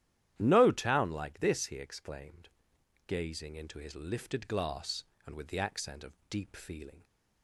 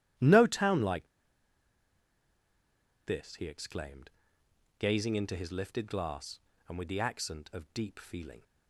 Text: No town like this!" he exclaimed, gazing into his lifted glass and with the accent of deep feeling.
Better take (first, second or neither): first